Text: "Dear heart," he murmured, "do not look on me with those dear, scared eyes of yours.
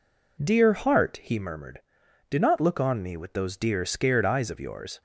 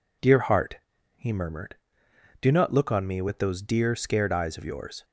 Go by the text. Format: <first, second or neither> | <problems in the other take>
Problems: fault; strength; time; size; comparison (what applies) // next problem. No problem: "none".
neither | none